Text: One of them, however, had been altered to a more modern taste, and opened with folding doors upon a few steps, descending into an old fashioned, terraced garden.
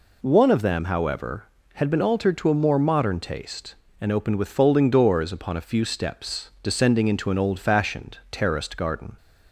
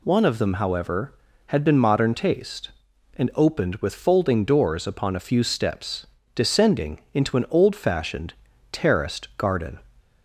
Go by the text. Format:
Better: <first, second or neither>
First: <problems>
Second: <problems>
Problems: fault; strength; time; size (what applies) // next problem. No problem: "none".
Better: first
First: none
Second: skips "altered to a more"; at 1.7 s